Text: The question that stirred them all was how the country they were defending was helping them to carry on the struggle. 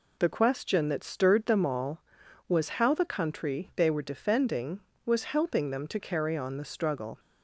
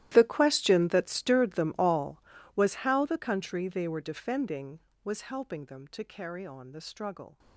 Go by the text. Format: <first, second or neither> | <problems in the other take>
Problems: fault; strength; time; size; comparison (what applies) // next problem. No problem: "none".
first | gets quieter; strong; throughout; 19.5 dB